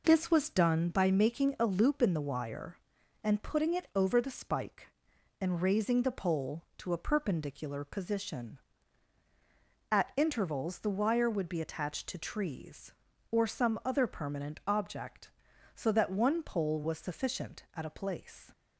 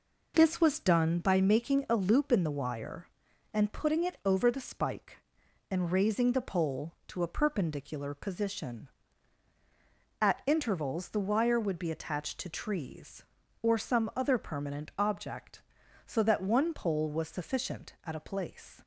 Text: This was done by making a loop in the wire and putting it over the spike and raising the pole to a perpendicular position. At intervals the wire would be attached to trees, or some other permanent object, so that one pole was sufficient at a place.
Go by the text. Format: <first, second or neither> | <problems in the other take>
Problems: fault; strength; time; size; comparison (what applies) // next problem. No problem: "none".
neither | none